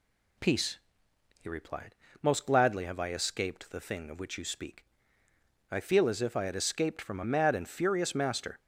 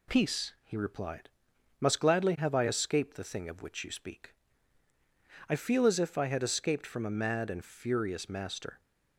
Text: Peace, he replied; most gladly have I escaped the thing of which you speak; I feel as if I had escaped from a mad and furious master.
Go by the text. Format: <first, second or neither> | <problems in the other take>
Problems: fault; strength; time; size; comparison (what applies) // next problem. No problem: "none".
first | says "must" for "most"; at 1.7 s